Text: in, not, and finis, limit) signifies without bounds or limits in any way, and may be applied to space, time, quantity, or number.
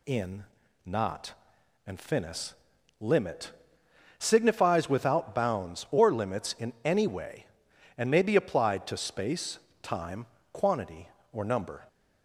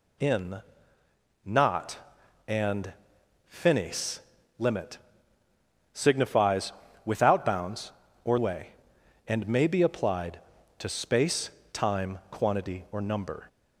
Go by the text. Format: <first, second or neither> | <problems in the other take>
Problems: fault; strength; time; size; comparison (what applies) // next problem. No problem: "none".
first | pauses between "and" and "finis"; noticeable; at 2.9 s; 0.56 s long // pauses between "signifies" and "without"; slight; at 6.7 s; 0.32 s long // skips "limits in any"; at 8.3 s